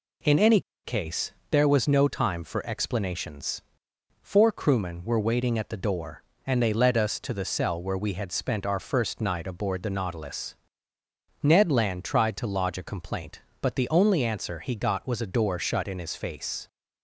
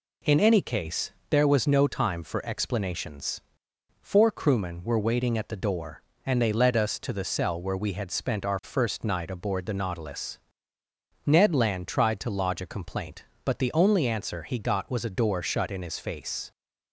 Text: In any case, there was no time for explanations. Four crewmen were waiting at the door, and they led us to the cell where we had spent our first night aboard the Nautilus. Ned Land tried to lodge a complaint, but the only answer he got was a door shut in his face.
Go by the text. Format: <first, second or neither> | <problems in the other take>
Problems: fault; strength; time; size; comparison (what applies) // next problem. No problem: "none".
second | pauses between "any" and "case"; slight; at 0.5 s; 0.24 s long